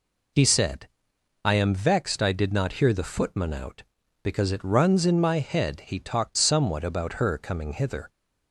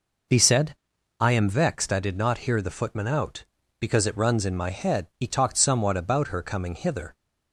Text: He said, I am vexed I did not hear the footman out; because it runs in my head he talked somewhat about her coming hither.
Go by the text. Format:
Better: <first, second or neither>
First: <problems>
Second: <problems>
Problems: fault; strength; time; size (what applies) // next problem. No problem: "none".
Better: neither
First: none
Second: none